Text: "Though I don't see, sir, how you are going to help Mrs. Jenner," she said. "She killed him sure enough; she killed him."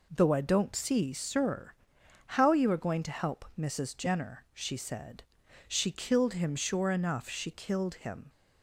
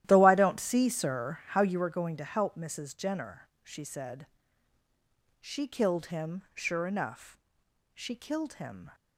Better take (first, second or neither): first